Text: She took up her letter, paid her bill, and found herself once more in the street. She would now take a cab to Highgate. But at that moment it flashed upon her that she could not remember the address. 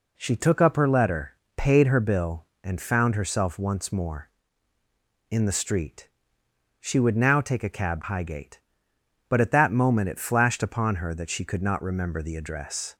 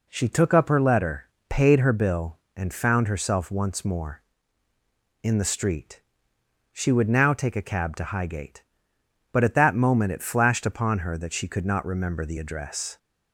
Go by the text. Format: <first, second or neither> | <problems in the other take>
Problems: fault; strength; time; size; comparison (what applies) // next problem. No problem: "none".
second | skips "to"; at 8.0 s